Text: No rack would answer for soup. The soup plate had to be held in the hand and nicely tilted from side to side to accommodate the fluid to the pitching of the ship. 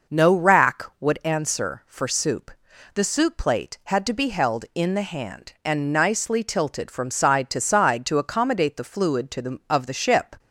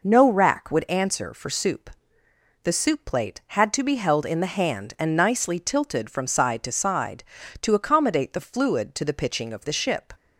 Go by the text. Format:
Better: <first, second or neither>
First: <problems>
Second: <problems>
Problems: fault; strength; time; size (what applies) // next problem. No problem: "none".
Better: second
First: skips "pitching"; at 9.6 s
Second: none